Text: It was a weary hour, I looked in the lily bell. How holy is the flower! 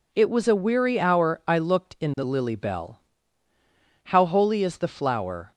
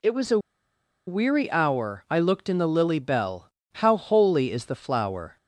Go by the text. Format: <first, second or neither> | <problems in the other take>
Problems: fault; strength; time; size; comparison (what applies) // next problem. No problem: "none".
first | pauses between "a" and "weary"; noticeable; at 0.3 s; 0.69 s long